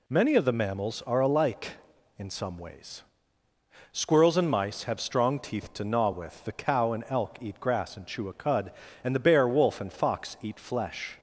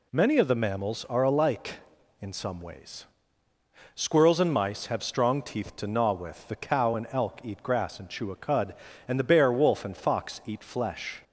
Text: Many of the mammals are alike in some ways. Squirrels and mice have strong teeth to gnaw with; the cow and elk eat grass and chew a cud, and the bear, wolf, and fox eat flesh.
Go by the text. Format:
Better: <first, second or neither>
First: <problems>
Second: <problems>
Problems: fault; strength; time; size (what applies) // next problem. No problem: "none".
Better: neither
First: none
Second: none